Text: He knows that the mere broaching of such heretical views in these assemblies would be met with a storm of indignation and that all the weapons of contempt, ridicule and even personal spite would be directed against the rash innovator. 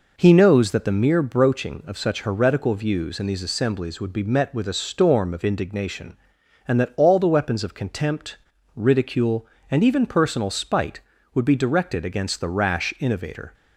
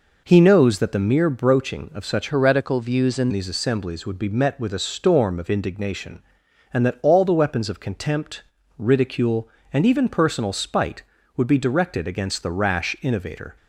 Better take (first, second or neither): first